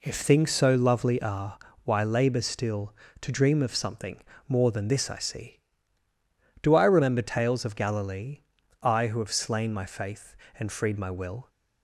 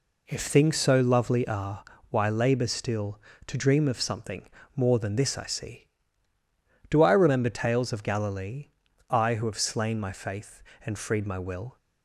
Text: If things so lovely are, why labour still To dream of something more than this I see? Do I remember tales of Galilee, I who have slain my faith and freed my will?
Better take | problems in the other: neither | pauses between "something" and "more"; slight; the same in both

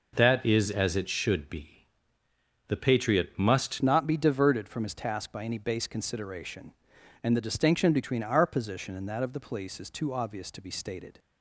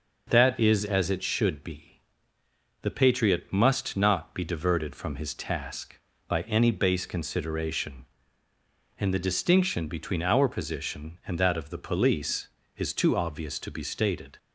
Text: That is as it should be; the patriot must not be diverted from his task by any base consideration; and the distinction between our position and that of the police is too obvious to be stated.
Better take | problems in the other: second | changes voice at "not"; from 3.8 s on; 7.3 s long

